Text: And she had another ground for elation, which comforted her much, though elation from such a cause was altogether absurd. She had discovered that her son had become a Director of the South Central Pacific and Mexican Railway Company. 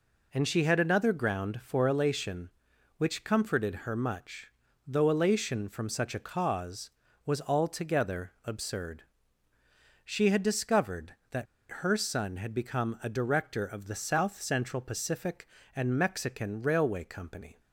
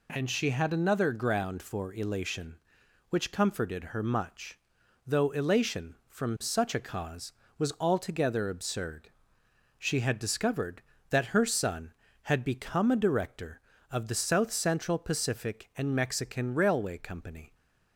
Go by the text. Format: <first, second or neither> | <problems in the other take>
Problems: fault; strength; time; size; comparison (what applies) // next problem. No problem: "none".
second | pauses between "that" and "her"; slight; at 11.4 s; 0.26 s long